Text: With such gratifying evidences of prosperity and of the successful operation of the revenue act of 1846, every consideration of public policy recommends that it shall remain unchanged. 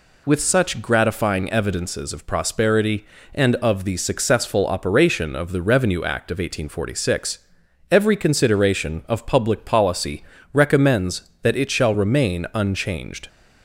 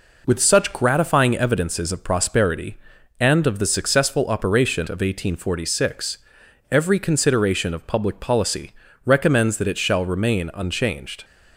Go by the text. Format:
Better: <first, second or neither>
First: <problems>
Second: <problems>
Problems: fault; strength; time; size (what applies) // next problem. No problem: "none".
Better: first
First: pauses between "policy" and "recommends"; slight; at 10.2 s; 0.28 s long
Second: skips "of the revenue act"; at 4.8 s // pauses between "policy" and "recommends"; slight; at 8.7 s; 0.30 s long